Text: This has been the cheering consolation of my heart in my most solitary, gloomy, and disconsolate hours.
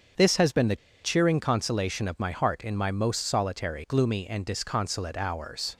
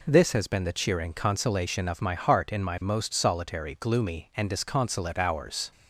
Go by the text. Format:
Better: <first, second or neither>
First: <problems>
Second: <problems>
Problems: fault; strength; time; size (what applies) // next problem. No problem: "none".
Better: second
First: starts louder than the rest; until 1.4 s; 7 dB // pauses between "the" and "cheering"; slight; at 0.7 s; 0.27 s long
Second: none